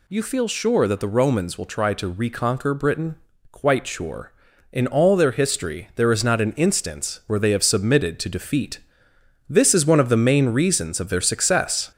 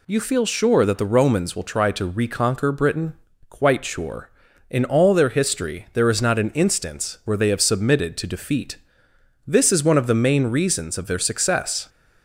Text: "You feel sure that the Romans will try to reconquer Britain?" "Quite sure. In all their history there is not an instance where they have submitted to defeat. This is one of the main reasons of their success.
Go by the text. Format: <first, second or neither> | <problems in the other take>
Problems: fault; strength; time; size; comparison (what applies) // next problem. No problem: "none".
second | gets louder; noticeable; throughout; 4.5 dB